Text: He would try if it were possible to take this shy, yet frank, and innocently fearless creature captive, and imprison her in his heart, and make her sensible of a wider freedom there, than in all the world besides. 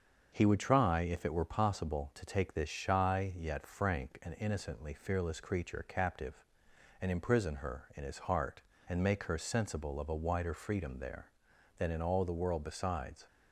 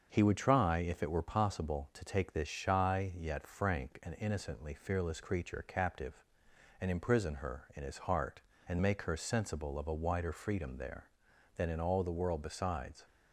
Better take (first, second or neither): neither